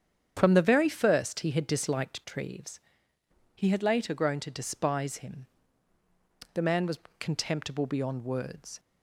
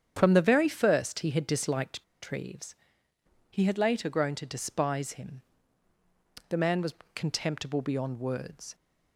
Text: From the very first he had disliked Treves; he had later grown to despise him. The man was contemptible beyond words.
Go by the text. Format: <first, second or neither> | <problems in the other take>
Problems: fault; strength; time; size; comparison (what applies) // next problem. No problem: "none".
first | starts louder than the rest; strong; until 1.1 s; 8 dB; strong in the first // pauses between "disliked" and "Treves"; slight; at 2.0 s; 0.18 s long // pauses between "was" and "contemptible"; slight; at 6.9 s; 0.22 s long; slight in the first